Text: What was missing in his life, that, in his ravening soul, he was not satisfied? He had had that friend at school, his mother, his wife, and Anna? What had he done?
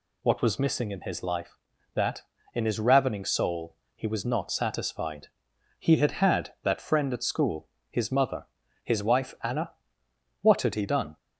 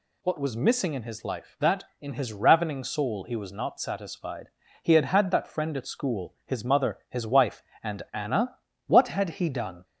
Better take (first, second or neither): second